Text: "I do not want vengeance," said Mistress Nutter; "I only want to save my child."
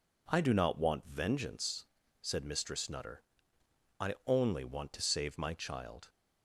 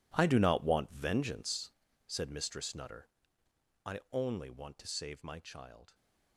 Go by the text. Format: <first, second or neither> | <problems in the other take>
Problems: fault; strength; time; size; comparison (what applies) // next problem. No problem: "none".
first | gets quieter; strong; throughout; 16 dB